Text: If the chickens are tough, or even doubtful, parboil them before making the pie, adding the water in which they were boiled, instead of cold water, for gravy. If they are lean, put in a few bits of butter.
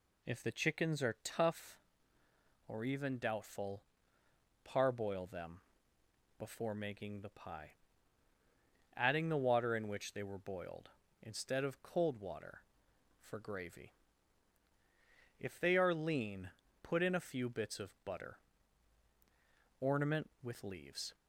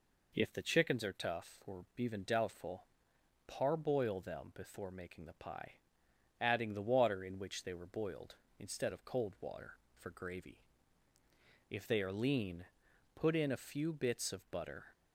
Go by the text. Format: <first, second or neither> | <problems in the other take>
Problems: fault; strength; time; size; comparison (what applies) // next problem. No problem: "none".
second | pauses between "them" and "before"; noticeable; at 5.6 s; 0.76 s long // goes on to say "Ornament with leaves"; from 19.7 s on; 1.3 s long